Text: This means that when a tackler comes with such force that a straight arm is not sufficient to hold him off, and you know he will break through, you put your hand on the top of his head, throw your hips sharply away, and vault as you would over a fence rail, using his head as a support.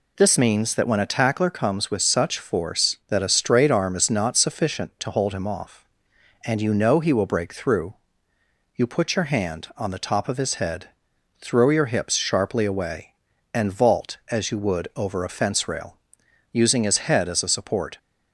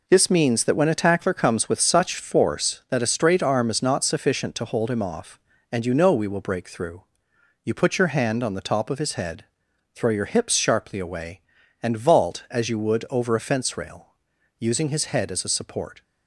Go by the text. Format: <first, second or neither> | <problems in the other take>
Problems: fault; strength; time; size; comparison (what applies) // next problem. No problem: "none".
first | says "we" for "he"; at 6.1 s